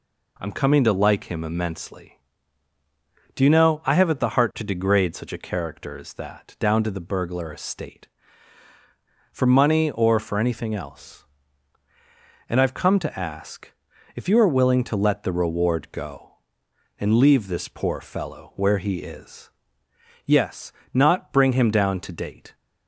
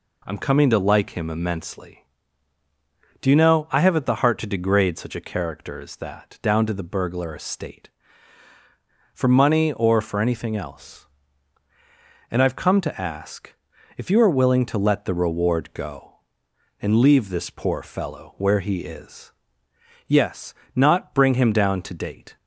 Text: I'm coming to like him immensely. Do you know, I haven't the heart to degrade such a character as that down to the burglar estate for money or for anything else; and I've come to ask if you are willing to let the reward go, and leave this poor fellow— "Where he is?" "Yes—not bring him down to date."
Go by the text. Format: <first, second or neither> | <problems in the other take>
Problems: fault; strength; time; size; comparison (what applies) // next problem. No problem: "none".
neither | pauses between "ask" and "if"; the same in both